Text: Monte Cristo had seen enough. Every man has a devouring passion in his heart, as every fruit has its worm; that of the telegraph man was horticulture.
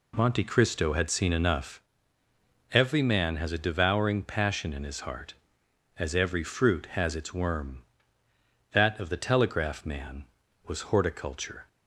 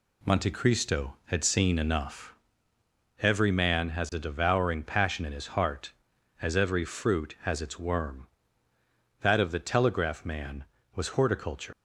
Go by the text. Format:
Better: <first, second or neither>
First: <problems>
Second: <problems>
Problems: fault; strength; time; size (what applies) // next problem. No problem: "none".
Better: first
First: none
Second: leaves "horticulture" unfinished; at 11.7 s; 95 ms